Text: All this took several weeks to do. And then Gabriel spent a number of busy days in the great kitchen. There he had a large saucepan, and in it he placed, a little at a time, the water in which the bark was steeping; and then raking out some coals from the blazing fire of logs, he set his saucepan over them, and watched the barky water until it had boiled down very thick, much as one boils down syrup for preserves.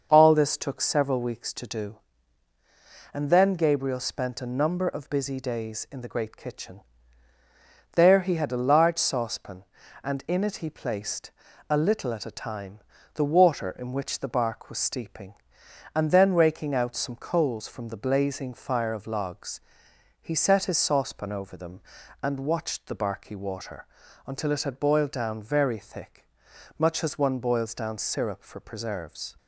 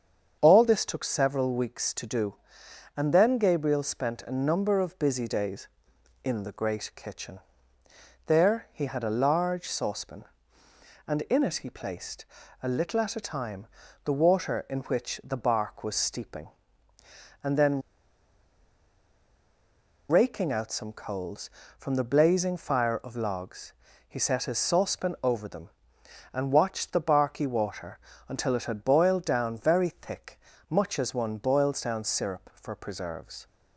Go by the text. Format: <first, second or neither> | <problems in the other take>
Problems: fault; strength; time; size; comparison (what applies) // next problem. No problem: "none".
first | starts louder than the rest; strong; until 1.4 s; 7.5 dB; also in the first // pauses between "then" and "raking"; strong; at 17.8 s; 2.2 s long // pauses between "water" and "until"; slight; at 27.9 s; 0.30 s long; also in the first